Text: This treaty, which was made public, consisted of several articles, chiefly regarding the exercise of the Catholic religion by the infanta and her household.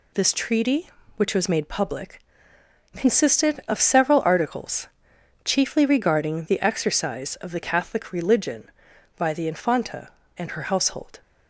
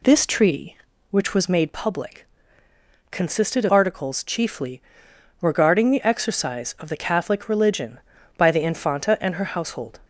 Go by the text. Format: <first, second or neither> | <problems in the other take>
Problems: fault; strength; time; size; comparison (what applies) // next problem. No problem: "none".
first | skips "several"; at 3.7 s // pauses between "chiefly" and "regarding"; noticeable; at 4.8 s; 0.60 s long